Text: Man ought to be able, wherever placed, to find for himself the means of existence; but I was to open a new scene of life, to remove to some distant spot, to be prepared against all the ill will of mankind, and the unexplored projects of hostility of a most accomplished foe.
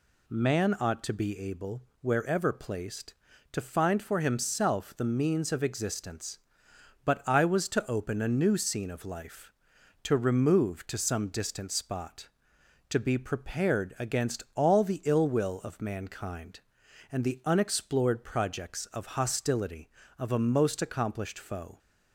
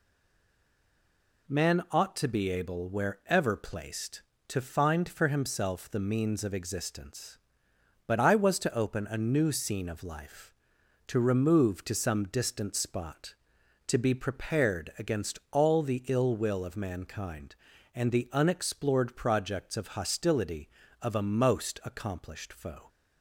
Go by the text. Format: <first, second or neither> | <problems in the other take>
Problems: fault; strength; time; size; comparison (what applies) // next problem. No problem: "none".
first | stays silent before the first word; noticeable; until 1.4 s; 1.4 s long